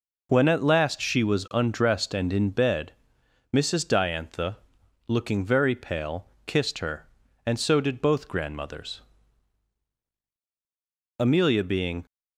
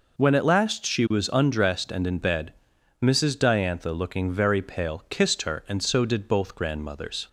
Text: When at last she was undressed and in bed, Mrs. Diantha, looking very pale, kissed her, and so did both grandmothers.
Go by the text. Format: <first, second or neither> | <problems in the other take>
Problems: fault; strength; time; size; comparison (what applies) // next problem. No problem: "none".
second | goes on to say "Amelia being"; noticeable; from 11.1 s on; 0.86 s long